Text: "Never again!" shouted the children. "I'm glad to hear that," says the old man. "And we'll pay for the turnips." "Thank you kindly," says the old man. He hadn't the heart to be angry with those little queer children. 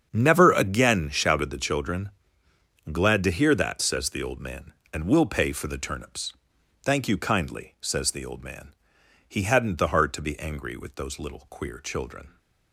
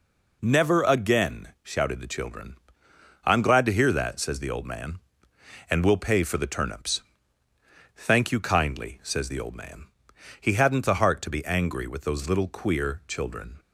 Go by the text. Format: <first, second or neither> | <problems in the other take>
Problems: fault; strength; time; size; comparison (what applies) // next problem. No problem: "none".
second | starts louder than the rest; strong; until 1.1 s; 7.5 dB // skips "I'm"; at 2.4 s